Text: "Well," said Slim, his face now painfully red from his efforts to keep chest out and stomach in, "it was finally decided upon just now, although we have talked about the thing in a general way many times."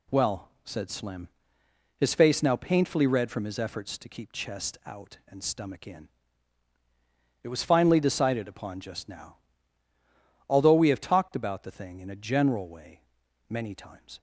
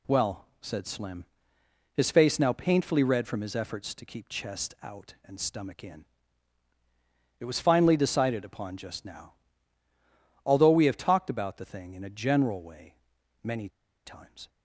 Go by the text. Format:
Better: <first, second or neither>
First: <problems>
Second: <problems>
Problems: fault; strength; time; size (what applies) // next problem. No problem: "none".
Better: first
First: pauses between "way" and "many"; noticeable; at 12.9 s; 0.48 s long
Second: pauses between "way" and "many"; noticeable; at 12.9 s; 0.48 s long // pauses between "many" and "times"; at 13.6 s; 0.37 s long